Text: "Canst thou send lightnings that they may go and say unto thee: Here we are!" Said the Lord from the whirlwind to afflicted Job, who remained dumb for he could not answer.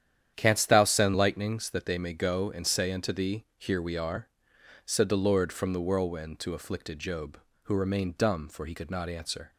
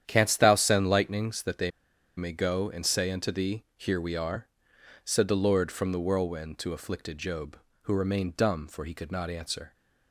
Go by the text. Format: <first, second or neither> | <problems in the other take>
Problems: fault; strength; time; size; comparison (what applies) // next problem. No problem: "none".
first | starts louder than the rest; strong; until 1.0 s; 9.5 dB; strong in the first // pauses between "they" and "may"; noticeable; at 1.6 s; 0.48 s long